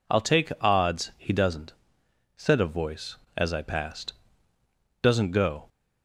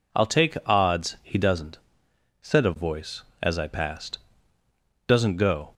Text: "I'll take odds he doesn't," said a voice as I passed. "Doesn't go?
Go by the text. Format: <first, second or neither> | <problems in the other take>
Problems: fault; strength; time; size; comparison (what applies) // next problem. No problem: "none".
neither | none